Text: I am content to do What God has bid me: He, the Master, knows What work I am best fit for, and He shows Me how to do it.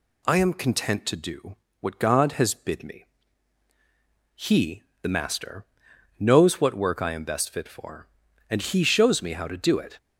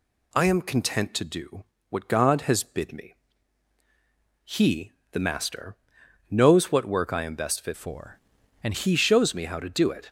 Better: first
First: pauses between "do" and "What"; slight; at 1.5 s; 0.25 s long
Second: pauses between "do" and "What"; slight; at 1.6 s; 0.26 s long // changes voice from "for" to "and"; from 7.7 to 8.7 s; 1.0 s long

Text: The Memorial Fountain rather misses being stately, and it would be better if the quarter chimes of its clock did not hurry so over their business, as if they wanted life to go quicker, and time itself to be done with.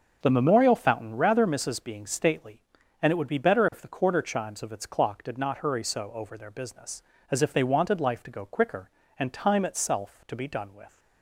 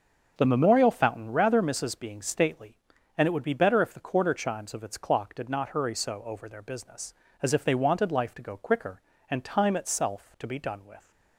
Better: neither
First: starts louder than the rest; until 1.2 s; 6.5 dB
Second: starts louder than the rest; until 1.3 s; 6.5 dB

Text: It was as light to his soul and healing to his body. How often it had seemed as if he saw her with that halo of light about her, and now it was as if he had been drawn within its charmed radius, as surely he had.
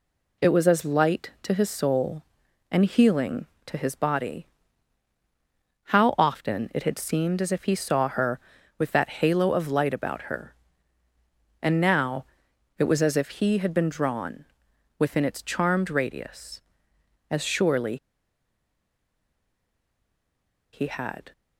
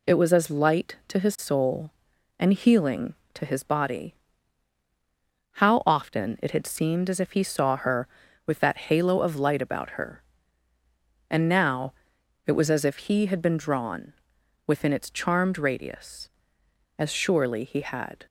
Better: second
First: pauses between "now" and "it"; noticeable; at 12.2 s; 0.54 s long // pauses between "drawn" and "within"; noticeable; at 14.4 s; 0.56 s long // pauses between "surely" and "he"; strong; at 17.9 s; 2.7 s long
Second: pauses between "now" and "it"; noticeable; at 11.9 s; 0.54 s long // pauses between "drawn" and "within"; noticeable; at 14.1 s; 0.56 s long

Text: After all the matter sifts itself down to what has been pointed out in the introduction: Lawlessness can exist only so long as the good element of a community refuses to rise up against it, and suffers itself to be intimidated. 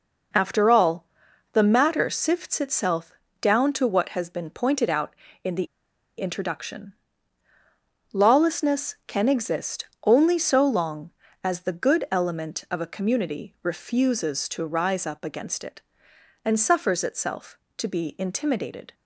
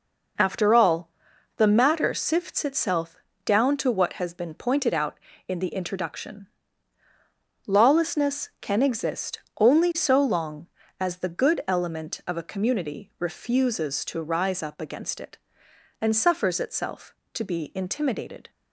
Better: second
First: pauses between "all" and "the"; noticeable; at 1.0 s; 0.48 s long // pauses between "itself" and "down"; slight; at 3.1 s; 0.30 s long // pauses between "the" and "introduction"; noticeable; at 5.6 s; 0.52 s long // pauses between "exist" and "only"; slight; at 9.8 s; 0.18 s long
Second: pauses between "all" and "the"; noticeable; at 1.0 s; 0.48 s long // pauses between "itself" and "down"; slight; at 3.1 s; 0.30 s long // pauses between "exist" and "only"; slight; at 9.3 s; 0.18 s long

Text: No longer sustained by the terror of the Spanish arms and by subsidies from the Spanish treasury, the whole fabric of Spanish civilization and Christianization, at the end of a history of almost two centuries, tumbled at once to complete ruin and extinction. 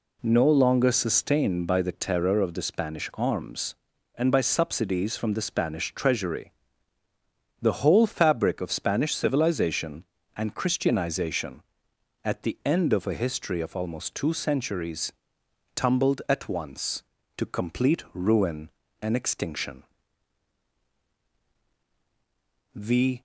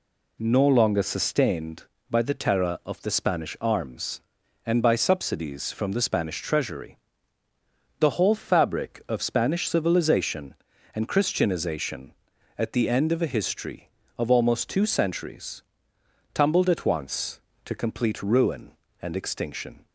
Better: second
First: goes on to say "The"; slight; from 22.7 s on; 0.46 s long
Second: none

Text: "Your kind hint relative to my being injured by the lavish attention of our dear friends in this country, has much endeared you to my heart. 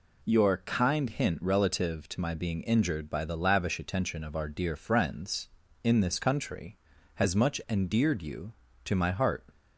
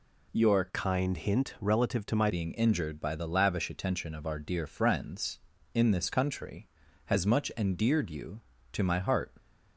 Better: first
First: none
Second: changes voice from "kind" to "my"; from 0.6 to 2.2 s; 1.6 s long

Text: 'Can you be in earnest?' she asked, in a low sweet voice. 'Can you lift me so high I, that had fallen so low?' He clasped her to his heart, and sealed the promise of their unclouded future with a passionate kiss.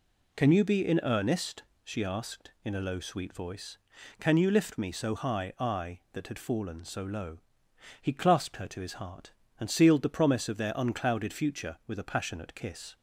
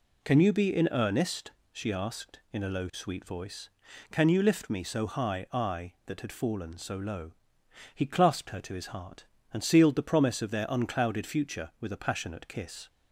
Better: neither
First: none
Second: none

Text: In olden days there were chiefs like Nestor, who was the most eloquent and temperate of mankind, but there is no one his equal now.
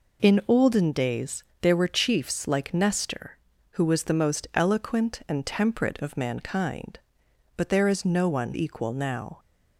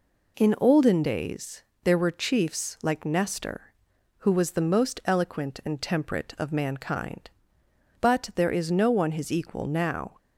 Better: second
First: pauses between "days" and "there"; slight; at 1.4 s; 0.20 s long // skips "his"; at 8.5 s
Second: pauses between "days" and "there"; slight; at 1.6 s; 0.22 s long

